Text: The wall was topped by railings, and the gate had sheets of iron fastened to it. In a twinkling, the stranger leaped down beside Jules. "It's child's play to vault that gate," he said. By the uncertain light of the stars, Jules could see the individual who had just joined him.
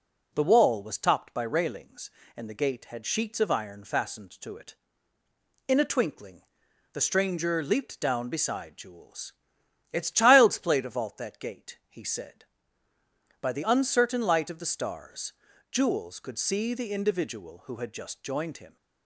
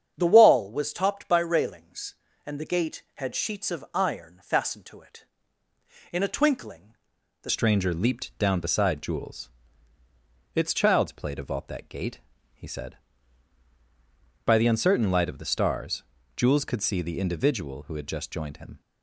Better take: first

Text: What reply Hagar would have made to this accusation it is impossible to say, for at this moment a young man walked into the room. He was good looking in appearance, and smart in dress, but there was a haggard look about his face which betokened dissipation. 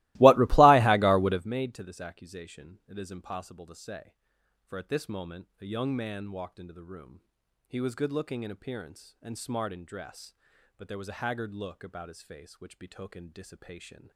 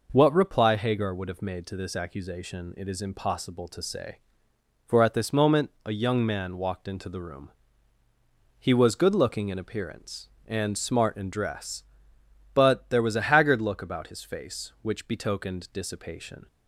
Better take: second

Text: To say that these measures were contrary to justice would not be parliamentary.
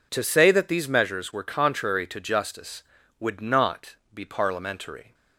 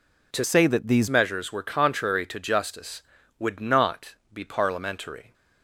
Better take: first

